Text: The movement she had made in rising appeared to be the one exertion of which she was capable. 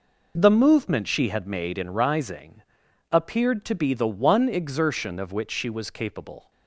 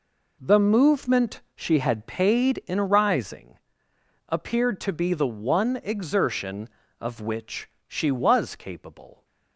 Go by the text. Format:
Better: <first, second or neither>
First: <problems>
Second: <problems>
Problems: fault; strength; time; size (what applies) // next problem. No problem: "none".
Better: first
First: pauses between "rising" and "appeared"; noticeable; at 2.6 s; 0.50 s long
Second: pauses between "movement" and "she"; slight; at 1.4 s; 0.16 s long // says "paid" for "made"; at 2.0 s // pauses between "rising" and "appeared"; noticeable; at 3.5 s; 0.70 s long // pauses between "which" and "she"; slight; at 7.6 s; 0.20 s long